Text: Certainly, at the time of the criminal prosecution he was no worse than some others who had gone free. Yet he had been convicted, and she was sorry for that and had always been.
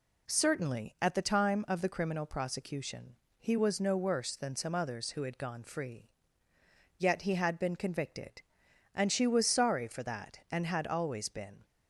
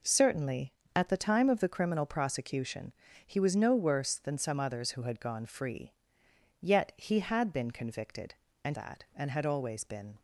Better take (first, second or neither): first